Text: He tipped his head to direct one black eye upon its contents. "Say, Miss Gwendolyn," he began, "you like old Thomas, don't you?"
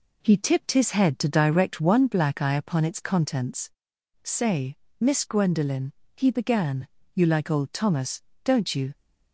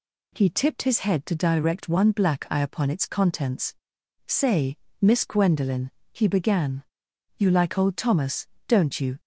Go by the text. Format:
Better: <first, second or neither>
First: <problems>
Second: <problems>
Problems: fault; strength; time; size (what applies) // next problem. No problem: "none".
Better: second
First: starts louder than the rest; slight; until 2.1 s; 3 dB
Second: none